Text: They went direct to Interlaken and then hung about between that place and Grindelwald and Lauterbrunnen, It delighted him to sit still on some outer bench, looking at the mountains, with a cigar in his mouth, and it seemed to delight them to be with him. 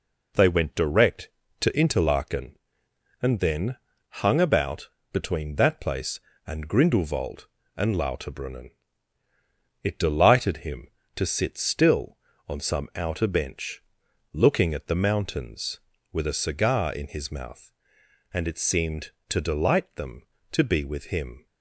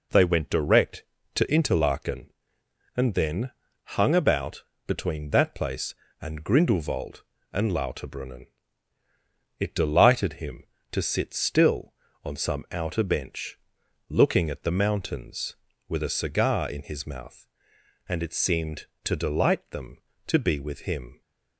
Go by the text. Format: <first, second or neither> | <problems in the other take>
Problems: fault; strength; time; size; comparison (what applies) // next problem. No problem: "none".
neither | pauses between "then" and "hung"; slight; the same in both // pauses between "about" and "between"; slight; the same in both